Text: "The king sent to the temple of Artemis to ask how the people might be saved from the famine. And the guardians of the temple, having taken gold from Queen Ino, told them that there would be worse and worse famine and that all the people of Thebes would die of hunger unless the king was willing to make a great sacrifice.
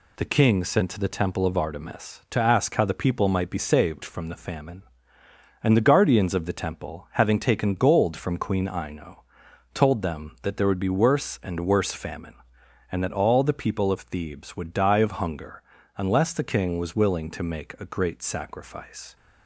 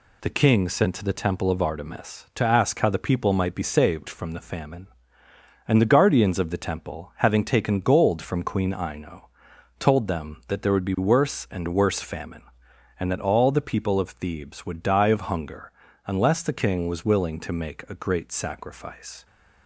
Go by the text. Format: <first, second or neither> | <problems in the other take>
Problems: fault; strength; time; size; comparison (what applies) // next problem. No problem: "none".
neither | pauses between "hunger" and "unless"; slight; the same in both